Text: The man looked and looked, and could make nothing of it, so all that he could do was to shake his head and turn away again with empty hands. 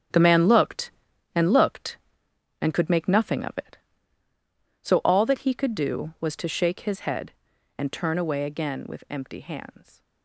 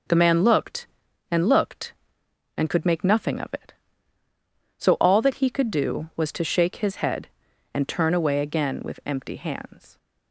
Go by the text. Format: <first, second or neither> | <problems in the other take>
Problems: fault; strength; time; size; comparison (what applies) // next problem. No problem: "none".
second | gets quieter; strong; throughout; 10.5 dB